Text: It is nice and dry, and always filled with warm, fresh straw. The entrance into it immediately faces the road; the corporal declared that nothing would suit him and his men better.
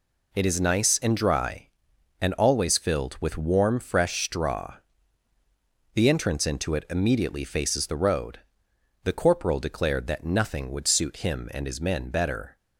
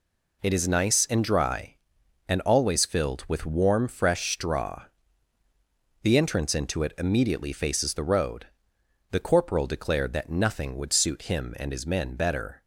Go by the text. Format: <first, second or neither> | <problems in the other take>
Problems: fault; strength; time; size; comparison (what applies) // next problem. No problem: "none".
neither | none